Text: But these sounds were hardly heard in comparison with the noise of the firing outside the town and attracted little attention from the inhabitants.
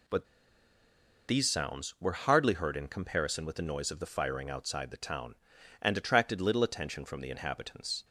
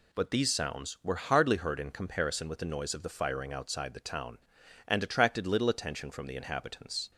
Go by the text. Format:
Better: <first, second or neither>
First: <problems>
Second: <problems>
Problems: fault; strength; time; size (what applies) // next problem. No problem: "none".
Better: second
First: pauses between "But" and "these"; at 0.2 s; 1.0 s long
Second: none